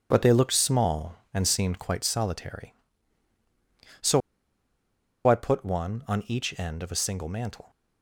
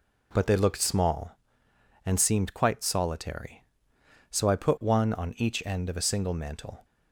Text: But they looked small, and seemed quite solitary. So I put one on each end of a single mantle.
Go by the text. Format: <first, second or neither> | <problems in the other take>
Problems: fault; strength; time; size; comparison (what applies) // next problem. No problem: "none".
second | pauses between "So" and "I"; at 4.2 s; 1.0 s long